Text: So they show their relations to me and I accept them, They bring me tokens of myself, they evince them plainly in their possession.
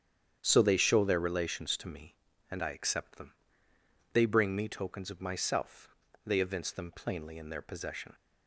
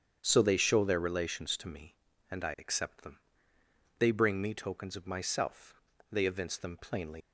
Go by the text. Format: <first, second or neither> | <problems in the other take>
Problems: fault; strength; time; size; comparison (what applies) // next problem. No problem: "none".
first | starts louder than the rest; strong; until 1.2 s; 8 dB; strong in the first // stops before "in their possession"; at 7.2 s